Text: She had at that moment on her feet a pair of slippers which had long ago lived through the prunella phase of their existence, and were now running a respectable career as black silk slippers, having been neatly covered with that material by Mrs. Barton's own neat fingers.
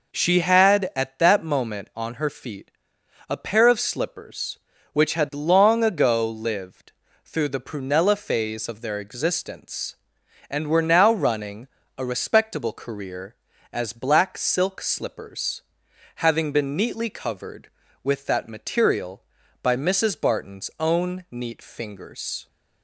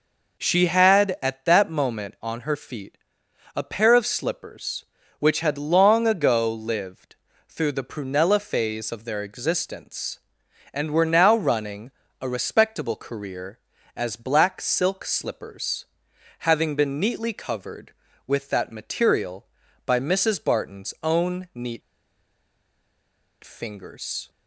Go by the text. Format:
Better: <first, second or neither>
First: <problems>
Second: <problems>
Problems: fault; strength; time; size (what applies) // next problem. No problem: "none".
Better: first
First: pauses between "feet" and "a"; noticeable; at 2.6 s; 0.60 s long // pauses between "lived" and "through"; slight; at 6.9 s; 0.32 s long // pauses between "running" and "a"; slight; at 11.6 s; 0.30 s long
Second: pauses between "feet" and "a"; noticeable; at 2.9 s; 0.60 s long // pauses between "lived" and "through"; slight; at 7.1 s; 0.32 s long // pauses between "running" and "a"; slight; at 11.9 s; 0.30 s long // pauses between "neat" and "fingers"; strong; at 21.8 s; 1.6 s long